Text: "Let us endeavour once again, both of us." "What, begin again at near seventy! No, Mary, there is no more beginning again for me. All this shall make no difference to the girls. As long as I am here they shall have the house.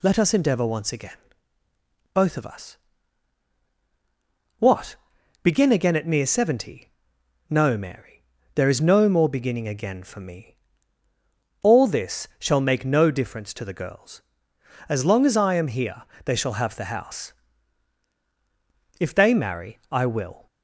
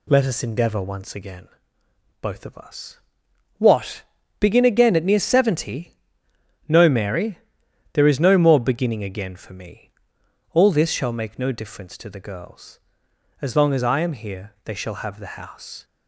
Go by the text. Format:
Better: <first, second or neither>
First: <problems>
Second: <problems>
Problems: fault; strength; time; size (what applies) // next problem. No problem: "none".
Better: second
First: pauses between "here" and "they"; slight; at 16.0 s; 0.24 s long // goes on to say "If they marry I will"; from 19.0 s on; 1.4 s long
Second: none